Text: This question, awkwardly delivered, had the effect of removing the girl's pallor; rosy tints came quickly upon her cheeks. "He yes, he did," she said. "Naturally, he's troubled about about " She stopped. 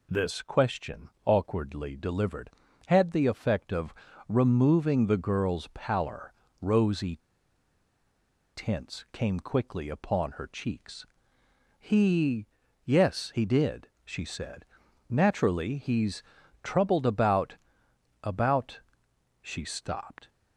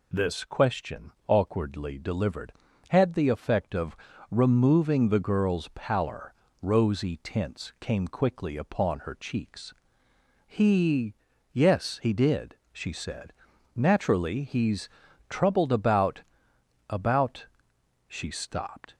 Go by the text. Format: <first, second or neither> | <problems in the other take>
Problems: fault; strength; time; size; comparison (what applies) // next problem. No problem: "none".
second | pauses between "of" and "removing"; slight; at 3.9 s; 0.34 s long; slight in the second // pauses between "rosy" and "tints"; strong; at 7.1 s; 1.3 s long // pauses between "He" and "yes"; at 12.4 s; 0.38 s long; also in the second // pauses between "he's" and "troubled"; at 16.2 s; 0.40 s long; also in the second // pauses between "about" and "about"; noticeable; at 17.5 s; 0.66 s long; noticeable in the second